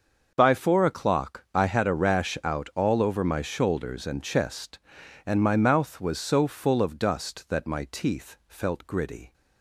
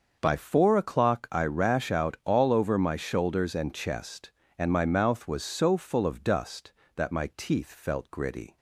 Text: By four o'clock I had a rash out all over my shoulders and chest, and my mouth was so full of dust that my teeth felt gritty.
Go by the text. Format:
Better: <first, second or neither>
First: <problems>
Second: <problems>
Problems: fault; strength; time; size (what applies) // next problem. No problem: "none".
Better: first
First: starts louder than the rest; until 1.3 s; 6.5 dB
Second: starts louder than the rest; until 1.2 s; 6.5 dB // skips "had a"; at 1.4 s